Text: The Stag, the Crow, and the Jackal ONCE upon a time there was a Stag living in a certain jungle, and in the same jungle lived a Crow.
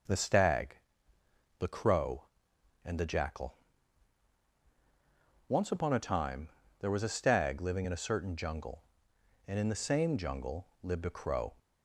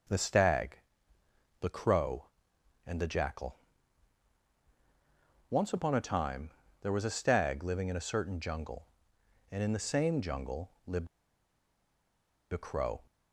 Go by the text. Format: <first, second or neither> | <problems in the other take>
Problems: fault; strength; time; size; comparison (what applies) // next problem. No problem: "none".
first | pauses between "Jackal" and "ONCE"; strong; at 3.5 s; 1.9 s long; strong in the first // pauses between "time" and "there"; slight; at 6.4 s; 0.30 s long; slight in the first // pauses between "lived" and "a"; strong; at 11.0 s; 1.4 s long